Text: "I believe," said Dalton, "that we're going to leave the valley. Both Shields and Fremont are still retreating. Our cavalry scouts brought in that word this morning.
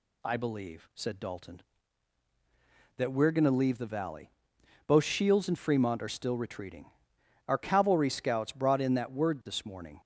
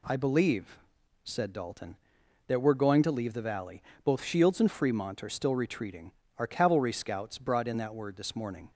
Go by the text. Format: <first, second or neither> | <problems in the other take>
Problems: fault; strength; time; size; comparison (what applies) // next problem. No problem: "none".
neither | none